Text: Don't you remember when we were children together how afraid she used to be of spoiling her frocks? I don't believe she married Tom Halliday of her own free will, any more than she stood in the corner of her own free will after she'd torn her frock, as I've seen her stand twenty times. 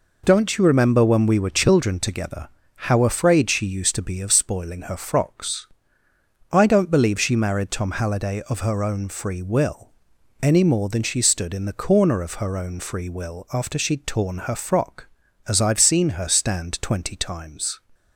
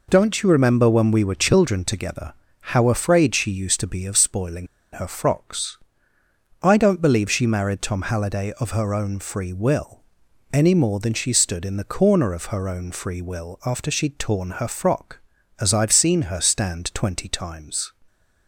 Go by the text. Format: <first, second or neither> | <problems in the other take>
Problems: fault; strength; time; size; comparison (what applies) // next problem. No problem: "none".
first | pauses between "together" and "how"; slight; at 2.3 s; 0.28 s long; slight in the first // pauses between "spoiling" and "her"; slight; at 4.6 s; 0.26 s long